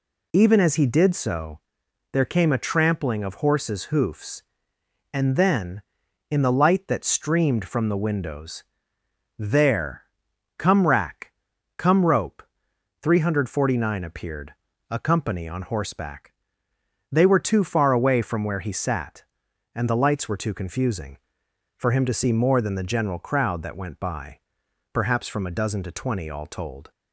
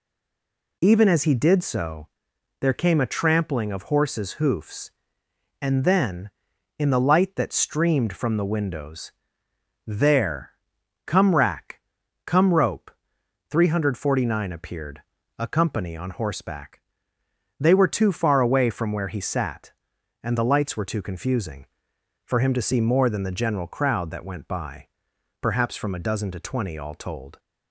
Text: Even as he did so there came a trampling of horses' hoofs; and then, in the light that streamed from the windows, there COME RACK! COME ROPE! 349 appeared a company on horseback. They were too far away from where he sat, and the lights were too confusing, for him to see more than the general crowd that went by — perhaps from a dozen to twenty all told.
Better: first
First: pauses between "so" and "there"; noticeable; at 1.5 s; 0.54 s long // pauses between "there" and "COME"; noticeable; at 10.0 s; 0.56 s long // pauses between "appeared" and "a"; slight; at 14.5 s; 0.36 s long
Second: stays silent before the first word; slight; until 0.8 s; 0.8 s long // pauses between "so" and "there"; noticeable; at 2.0 s; 0.54 s long // pauses between "there" and "COME"; noticeable; at 10.5 s; 0.56 s long // pauses between "appeared" and "a"; slight; at 15.0 s; 0.36 s long

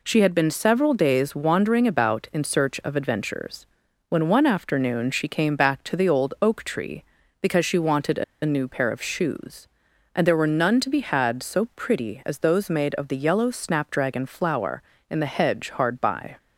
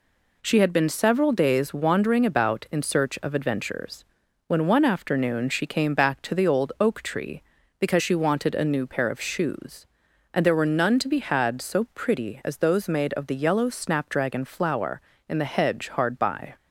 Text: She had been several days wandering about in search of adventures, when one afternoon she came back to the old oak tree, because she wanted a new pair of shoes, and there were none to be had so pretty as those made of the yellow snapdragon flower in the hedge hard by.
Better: second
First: pauses between "a" and "new"; slight; at 8.2 s; 0.20 s long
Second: none

